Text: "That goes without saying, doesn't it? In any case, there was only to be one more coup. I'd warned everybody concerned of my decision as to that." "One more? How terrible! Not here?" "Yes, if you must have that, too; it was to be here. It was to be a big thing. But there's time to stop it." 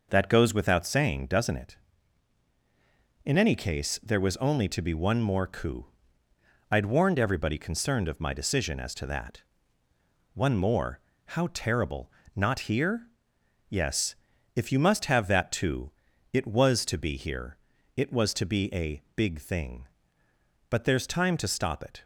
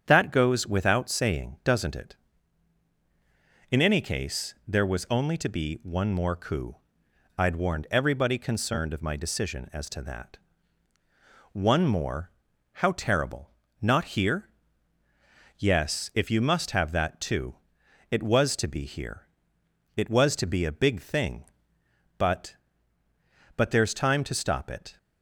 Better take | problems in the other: first | starts louder than the rest; strong; until 1.0 s; 8 dB // says "But" twice; at 23.5 s

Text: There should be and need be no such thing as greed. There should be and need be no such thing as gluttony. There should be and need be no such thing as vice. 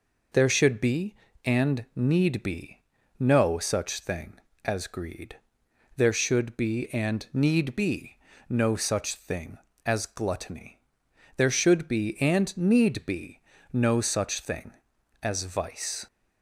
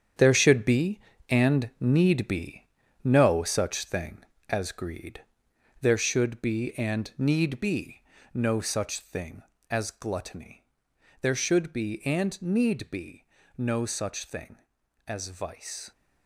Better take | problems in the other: first | gets quieter; strong; throughout; 9.5 dB // pauses between "be" and "no"; at 2.6 s; 0.38 s long; also in the first // pauses between "be" and "no"; slight; at 8.0 s; 0.32 s long; slight in the first // pauses between "be" and "no"; slight; at 13.2 s; 0.30 s long; slight in the first

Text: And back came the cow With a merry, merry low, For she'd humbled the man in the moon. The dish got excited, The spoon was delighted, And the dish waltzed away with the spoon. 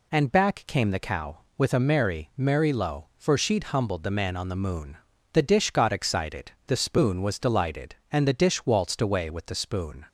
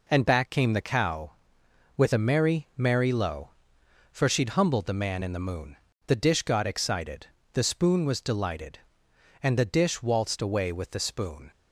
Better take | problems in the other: second | says "on" for "in"; at 4.3 s

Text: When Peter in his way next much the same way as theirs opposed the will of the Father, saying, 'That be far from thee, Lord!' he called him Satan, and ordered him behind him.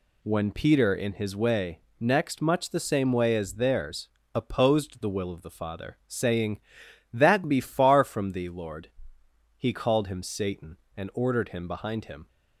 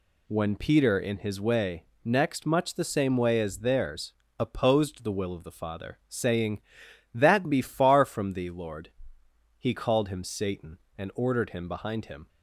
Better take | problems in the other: neither | pauses between "way" and "next"; slight; the same in both // pauses between "theirs" and "opposed"; slight; the same in both

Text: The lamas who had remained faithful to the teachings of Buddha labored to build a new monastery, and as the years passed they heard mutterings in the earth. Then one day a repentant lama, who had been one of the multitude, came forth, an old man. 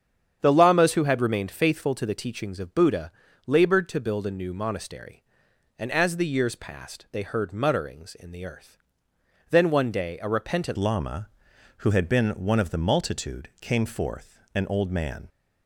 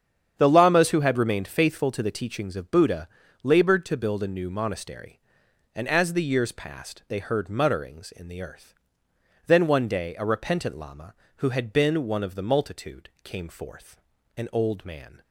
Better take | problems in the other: second | starts louder than the rest; strong; until 1.4 s; 8.5 dB; strong in the second // pauses between "Buddha" and "labored"; slight; at 3.1 s; 0.36 s long; slight in the second // changes voice at "lama"; from 10.7 s on; 4.5 s long

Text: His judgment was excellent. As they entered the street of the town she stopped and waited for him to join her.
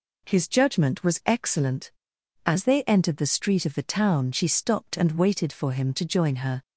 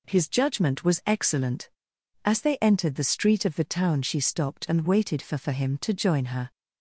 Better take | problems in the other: first | says "for" twice; at 5.3 s

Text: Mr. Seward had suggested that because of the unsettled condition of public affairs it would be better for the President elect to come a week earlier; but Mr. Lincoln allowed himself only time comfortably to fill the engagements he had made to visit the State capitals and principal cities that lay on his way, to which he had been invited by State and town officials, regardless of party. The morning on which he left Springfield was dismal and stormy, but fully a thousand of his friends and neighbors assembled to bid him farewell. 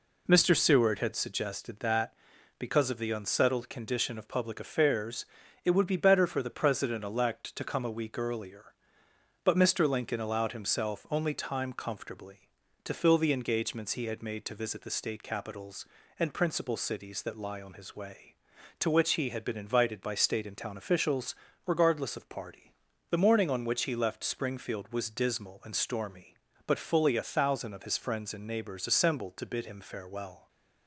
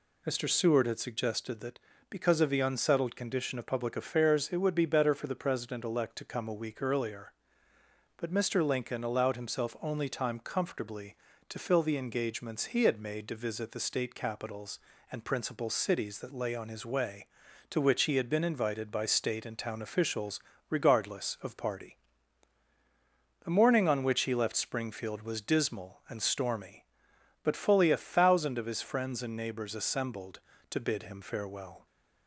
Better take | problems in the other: second | pauses between "affairs" and "it"; at 5.2 s; 0.40 s long // says "lie" for "lay"; at 17.3 s

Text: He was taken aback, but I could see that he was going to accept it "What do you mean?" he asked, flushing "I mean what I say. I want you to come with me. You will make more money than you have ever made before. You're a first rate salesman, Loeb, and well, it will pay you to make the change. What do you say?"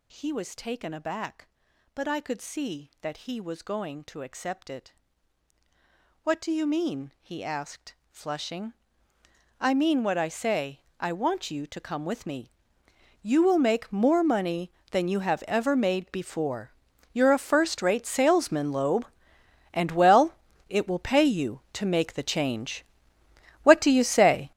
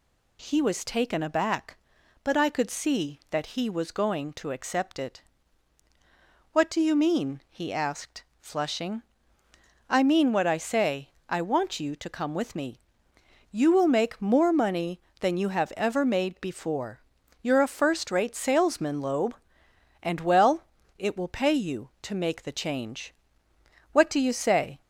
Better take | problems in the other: second | gets louder; strong; throughout; 13 dB // pauses between "it" and "What"; strong; at 4.9 s; 1.3 s long; strong in the second // pauses between "flushing" and "I"; noticeable; at 8.7 s; 0.88 s long; noticeable in the second

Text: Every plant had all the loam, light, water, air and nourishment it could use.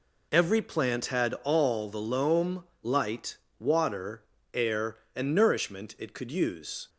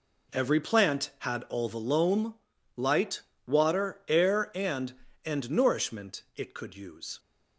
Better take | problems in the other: first | says "and" twice; at 5.2 s

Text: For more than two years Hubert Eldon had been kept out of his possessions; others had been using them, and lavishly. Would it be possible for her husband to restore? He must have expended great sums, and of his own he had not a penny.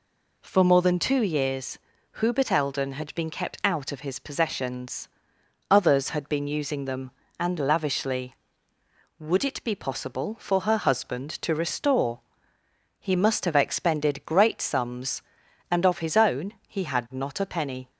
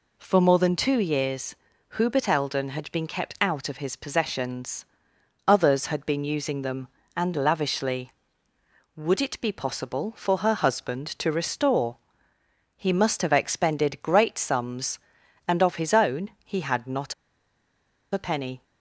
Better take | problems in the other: first | pauses between "years" and "Hubert"; at 1.5 s; 0.42 s long; also in the first // pauses between "not" and "a"; at 17.1 s; 0.99 s long

